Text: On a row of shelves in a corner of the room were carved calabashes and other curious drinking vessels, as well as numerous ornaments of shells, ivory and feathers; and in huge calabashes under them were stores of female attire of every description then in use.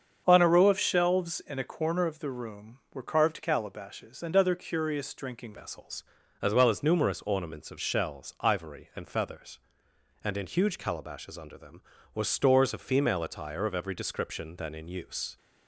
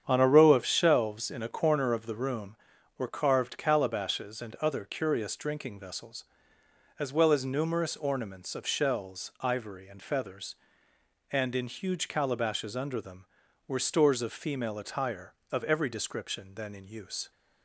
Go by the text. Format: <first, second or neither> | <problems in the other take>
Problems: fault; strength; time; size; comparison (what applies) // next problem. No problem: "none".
second | starts louder than the rest; strong; until 1.2 s; 7 dB; strong in the second // changes voice at "vessels"; from 5.5 s on; 9.8 s long